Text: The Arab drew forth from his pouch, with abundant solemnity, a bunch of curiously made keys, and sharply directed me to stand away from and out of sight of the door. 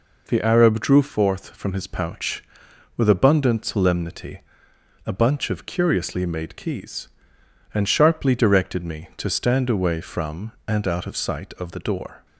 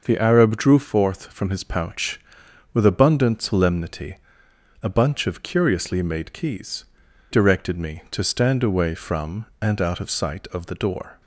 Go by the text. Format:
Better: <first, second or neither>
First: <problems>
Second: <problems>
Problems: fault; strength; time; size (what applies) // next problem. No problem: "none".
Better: first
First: none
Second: skips "and sharply"; at 7.0 s